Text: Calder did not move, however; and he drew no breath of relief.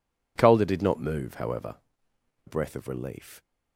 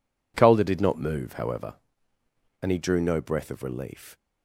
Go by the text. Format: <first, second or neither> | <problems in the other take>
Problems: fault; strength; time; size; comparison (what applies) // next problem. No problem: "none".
second | skips "and he drew no"; at 2.1 s